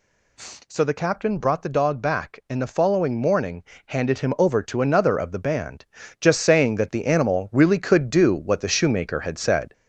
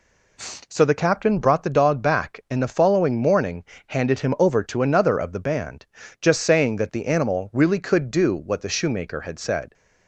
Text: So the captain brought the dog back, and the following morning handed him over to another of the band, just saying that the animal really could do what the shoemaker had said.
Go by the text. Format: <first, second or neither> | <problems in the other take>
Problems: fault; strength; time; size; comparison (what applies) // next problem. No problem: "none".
second | gets louder; slight; throughout; 3 dB // pauses between "morning" and "handed"; slight; at 3.6 s; 0.24 s long; slight in the second